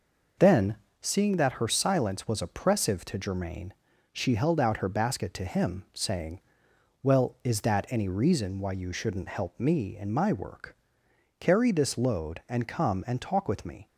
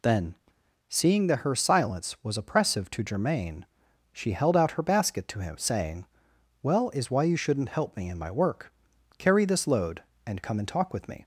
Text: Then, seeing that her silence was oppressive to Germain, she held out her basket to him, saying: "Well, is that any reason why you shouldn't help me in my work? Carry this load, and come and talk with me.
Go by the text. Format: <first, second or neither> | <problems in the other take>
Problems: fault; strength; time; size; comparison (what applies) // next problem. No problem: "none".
first | skips "that any reason"; at 7.1 s